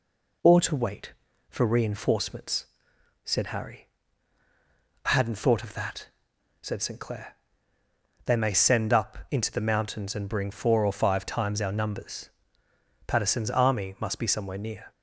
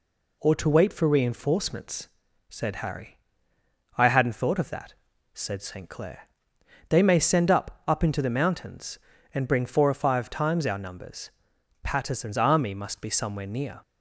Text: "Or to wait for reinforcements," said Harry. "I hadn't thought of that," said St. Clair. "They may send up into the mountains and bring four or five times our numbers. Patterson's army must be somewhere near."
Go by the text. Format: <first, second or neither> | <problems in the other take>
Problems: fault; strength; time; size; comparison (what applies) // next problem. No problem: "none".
first | says "up" twice; at 7.8 s